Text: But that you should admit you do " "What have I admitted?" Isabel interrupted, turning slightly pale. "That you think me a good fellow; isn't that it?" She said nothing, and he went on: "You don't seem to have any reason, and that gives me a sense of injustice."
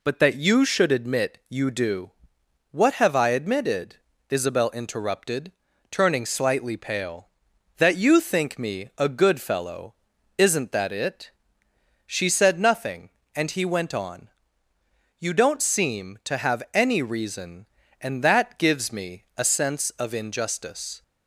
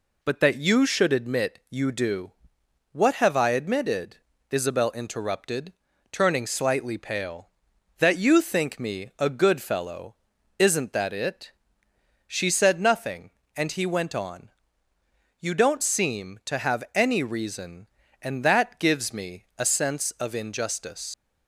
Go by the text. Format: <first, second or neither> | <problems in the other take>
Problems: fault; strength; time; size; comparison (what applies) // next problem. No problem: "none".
first | leaves "injustice" unfinished; at 21.1 s; 95 ms